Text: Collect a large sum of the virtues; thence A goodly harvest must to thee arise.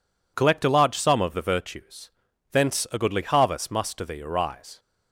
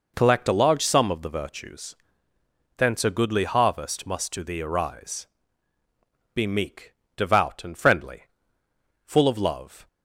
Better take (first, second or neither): first